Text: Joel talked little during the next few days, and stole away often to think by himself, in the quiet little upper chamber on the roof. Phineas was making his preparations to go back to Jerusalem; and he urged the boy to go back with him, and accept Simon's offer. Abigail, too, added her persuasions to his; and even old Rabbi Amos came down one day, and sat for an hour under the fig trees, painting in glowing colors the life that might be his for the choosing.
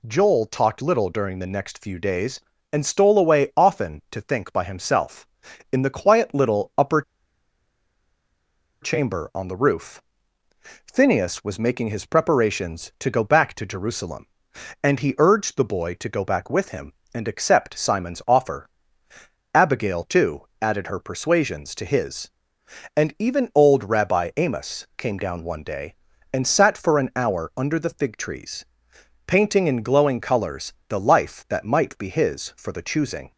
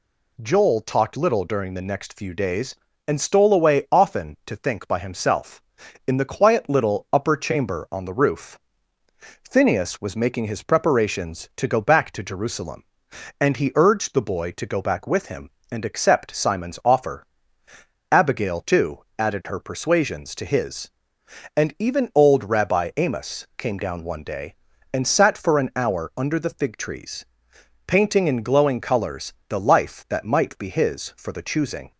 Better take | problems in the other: second | pauses between "upper" and "chamber"; strong; at 7.0 s; 1.8 s long // pauses between "colors" and "the"; slight; at 30.7 s; 0.16 s long; slight in the second

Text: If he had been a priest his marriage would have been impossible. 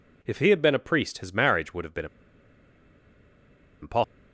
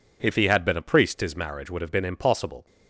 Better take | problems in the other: second | pauses between "been" and "impossible"; strong; at 2.0 s; 1.7 s long

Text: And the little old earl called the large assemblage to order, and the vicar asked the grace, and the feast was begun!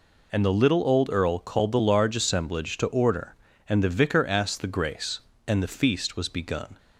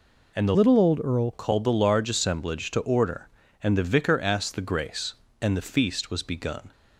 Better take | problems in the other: first | changes voice from "little" to "earl"; from 0.5 to 1.3 s; 0.8 s long

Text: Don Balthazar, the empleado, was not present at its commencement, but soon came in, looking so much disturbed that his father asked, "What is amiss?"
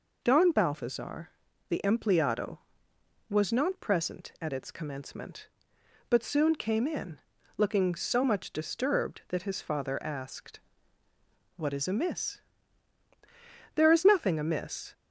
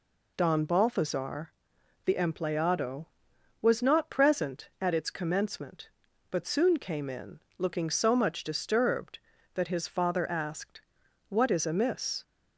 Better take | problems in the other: second | goes on to say "There is nothing amiss"; noticeable; from 13.7 s on; 1.1 s long

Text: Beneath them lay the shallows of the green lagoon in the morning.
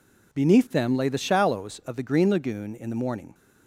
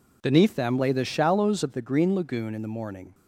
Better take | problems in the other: neither | none

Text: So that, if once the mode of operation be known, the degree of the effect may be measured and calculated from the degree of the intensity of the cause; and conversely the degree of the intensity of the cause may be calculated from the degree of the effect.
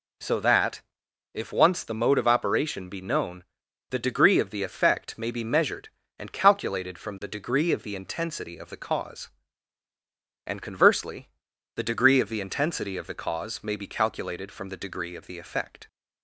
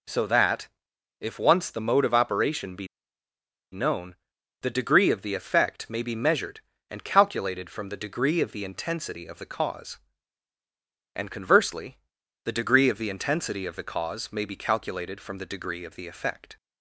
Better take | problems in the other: first | pauses between "be" and "known"; noticeable; at 2.8 s; 0.85 s long // pauses between "conversely" and "the"; noticeable; at 11.9 s; 0.46 s long; noticeable in the first

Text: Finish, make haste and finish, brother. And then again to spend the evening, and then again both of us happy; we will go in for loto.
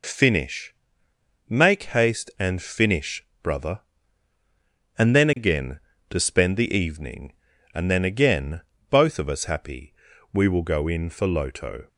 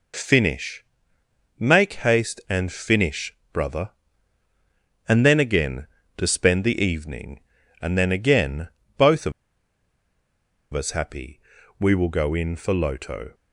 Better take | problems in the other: first | pauses between "again" and "both"; slight; at 8.6 s; 0.28 s long; slight in the first // pauses between "of" and "us"; strong; at 9.3 s; 1.4 s long

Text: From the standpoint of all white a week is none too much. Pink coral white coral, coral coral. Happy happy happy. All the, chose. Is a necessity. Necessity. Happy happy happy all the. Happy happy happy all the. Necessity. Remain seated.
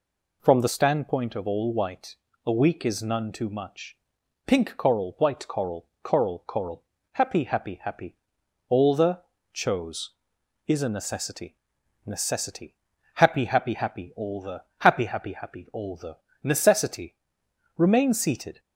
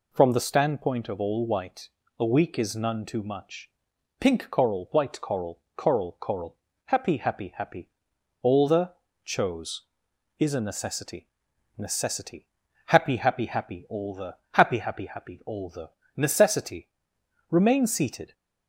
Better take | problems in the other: neither | pauses between "white" and "a"; slight; the same in both

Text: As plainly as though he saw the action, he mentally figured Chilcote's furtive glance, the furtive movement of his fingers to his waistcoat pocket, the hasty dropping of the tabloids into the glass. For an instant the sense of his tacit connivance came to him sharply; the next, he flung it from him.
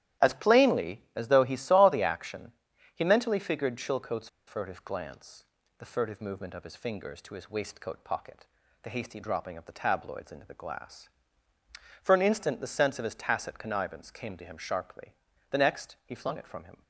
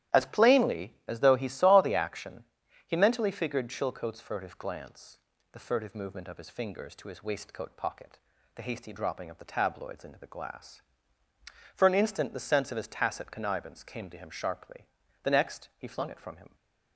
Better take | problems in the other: second | starts louder than the rest; strong; until 1.3 s; 12.5 dB; strong in the second // pauses between "Chilcote's" and "furtive"; slight; at 4.2 s; 0.20 s long

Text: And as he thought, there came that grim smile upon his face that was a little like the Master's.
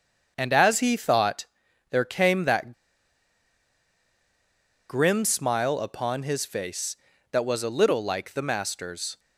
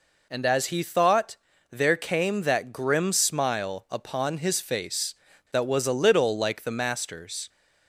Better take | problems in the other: second | starts louder than the rest; until 1.3 s; 7 dB // pauses between "that" and "grim"; strong; at 2.7 s; 2.1 s long

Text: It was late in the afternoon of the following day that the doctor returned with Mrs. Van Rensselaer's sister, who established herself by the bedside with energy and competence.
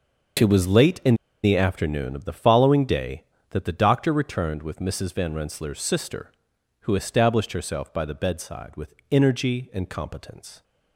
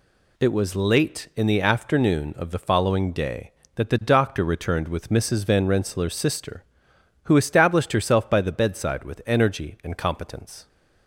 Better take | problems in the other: second | starts louder than the rest; noticeable; until 1.7 s; 6 dB // pauses between "in" and "the"; slight; at 1.1 s; 0.27 s long // pauses between "with" and "energy"; slight; at 8.9 s; 0.16 s long

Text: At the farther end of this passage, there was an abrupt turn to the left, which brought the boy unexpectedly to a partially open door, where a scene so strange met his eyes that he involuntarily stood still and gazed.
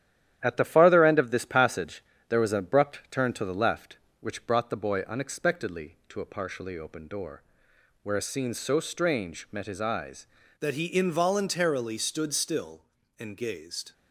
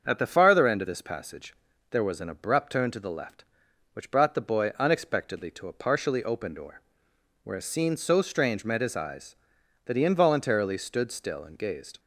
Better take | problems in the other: second | starts louder than the rest; strong; until 1.4 s; 11 dB; also in the second // changes voice at "that"; from 10.6 s on; 3.3 s long

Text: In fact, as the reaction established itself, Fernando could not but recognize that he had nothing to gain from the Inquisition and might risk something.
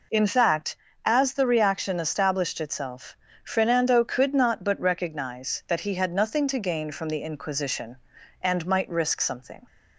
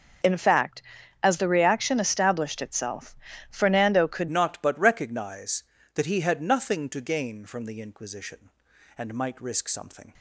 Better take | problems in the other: first | starts louder than the rest; noticeable; until 1.6 s; 6 dB // changes voice at "not"; from 4.2 s on; 5.9 s long

